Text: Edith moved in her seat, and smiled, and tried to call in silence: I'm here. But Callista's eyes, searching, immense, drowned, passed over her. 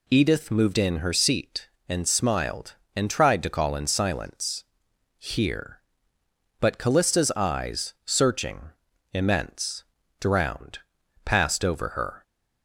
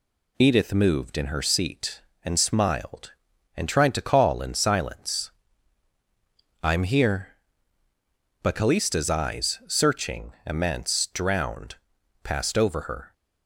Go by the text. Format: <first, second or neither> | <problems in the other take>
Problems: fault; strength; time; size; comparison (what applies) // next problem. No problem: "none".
second | skips "I'm"; at 4.9 s